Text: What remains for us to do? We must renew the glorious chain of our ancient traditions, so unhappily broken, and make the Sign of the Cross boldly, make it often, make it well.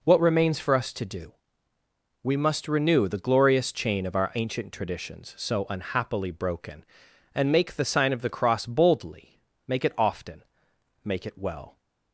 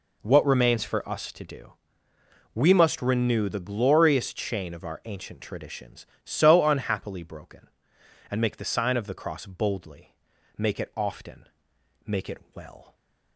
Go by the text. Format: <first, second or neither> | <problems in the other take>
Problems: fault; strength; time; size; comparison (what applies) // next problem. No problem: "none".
neither | none